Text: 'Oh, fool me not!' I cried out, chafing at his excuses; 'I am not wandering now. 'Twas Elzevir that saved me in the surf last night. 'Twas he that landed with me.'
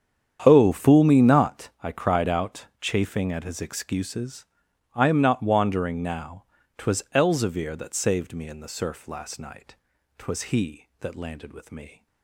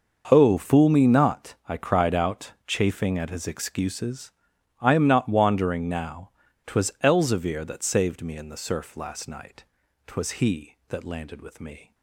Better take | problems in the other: second | starts louder than the rest; strong; until 1.9 s; 8.5 dB

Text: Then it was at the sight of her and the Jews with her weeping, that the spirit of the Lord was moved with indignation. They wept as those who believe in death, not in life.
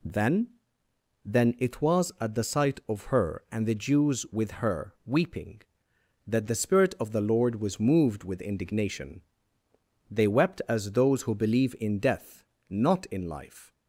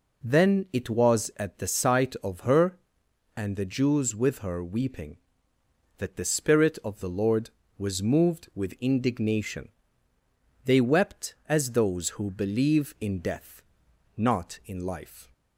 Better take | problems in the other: second | says "Then" twice; at 1.2 s

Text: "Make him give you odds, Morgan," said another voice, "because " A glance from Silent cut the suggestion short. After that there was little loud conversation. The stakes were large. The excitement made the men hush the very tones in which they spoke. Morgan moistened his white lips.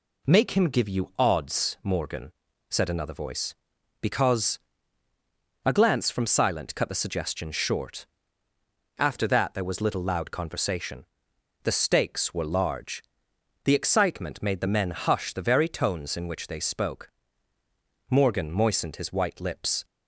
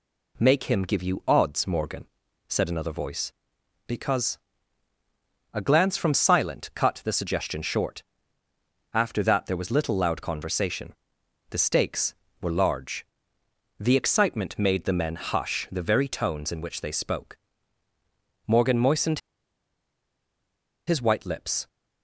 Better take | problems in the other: first | pauses between "moistened" and "his"; strong; at 19.1 s; 1.6 s long

